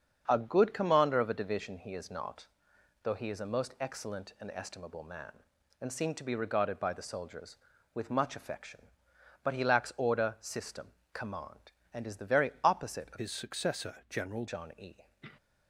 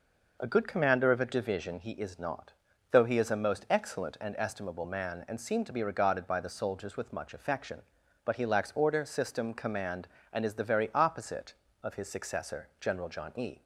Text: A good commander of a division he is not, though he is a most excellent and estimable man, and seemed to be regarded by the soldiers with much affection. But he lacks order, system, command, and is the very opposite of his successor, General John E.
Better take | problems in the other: second | starts louder than the rest; until 1.2 s; 7 dB // changes voice from "his" to "General"; from 13.1 to 14.4 s; 1.3 s long

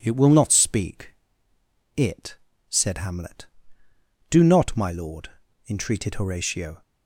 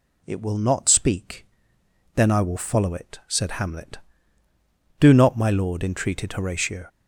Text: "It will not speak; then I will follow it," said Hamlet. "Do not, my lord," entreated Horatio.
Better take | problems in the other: second | skips "then I will follow"; at 1.5 s

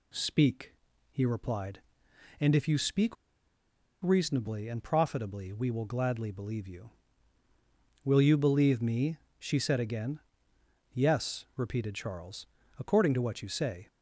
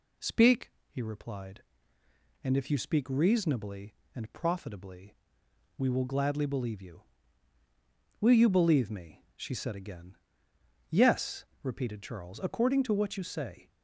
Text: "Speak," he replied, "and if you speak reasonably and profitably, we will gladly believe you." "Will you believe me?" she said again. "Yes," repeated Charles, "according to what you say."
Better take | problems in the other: second | pauses between "speak" and "reasonably"; noticeable; at 3.1 s; 0.88 s long

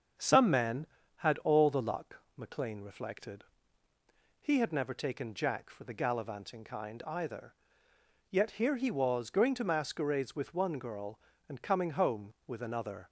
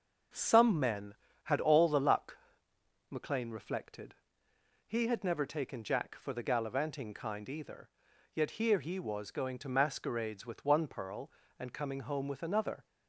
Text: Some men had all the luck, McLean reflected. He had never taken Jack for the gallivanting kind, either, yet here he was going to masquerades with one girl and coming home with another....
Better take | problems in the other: first | starts louder than the rest; until 1.6 s; 6.5 dB; also in the first // says "pearl" for "girl"; at 10.8 s

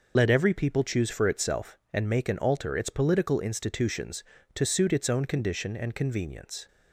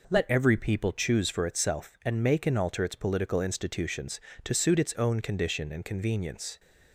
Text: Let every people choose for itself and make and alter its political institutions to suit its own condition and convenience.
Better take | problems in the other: second | loses the start of "Let"; at 0.1 s; 50 ms

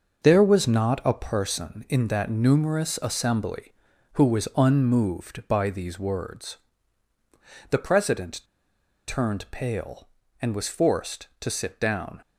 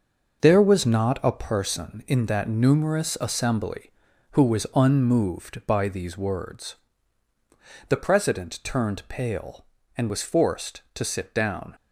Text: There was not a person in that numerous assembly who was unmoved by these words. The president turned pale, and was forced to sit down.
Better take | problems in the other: second | pauses between "president" and "turned"; noticeable; at 8.4 s; 0.65 s long

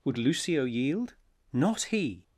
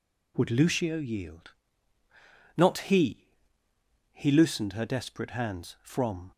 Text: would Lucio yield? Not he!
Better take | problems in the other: first | goes on to say "he loosened her desperate hands from"; strong; from 4.1 s on; 2.2 s long

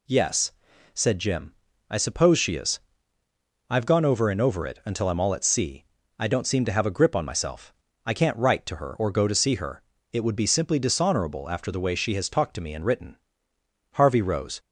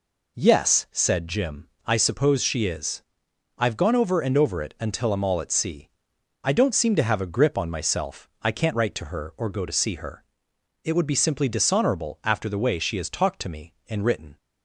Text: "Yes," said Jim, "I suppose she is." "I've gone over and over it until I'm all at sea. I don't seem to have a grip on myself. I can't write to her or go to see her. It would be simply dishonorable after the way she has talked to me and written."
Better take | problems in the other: second | goes on to say "Harvey rose"; noticeable; from 13.9 s on; 0.68 s long

